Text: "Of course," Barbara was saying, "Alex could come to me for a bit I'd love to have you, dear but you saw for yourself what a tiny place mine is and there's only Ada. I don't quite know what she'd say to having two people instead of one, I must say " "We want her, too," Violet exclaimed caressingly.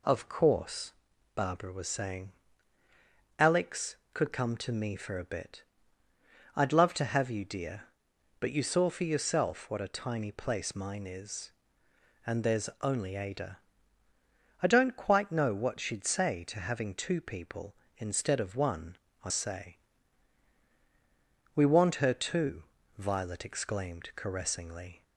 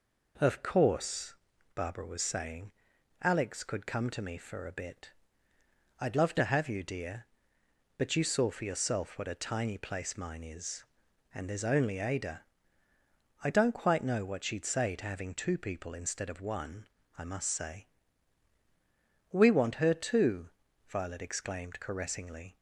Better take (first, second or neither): second